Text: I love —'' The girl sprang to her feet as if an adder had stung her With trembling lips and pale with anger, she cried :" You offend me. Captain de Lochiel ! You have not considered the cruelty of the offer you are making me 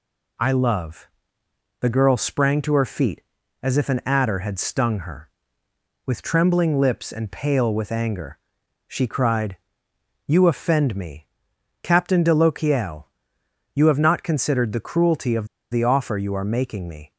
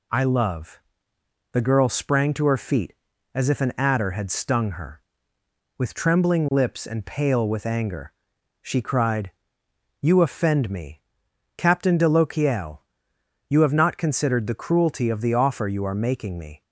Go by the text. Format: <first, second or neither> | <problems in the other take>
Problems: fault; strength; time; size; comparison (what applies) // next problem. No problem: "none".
second | pauses between "of" and "the"; slight; at 15.4 s; 0.26 s long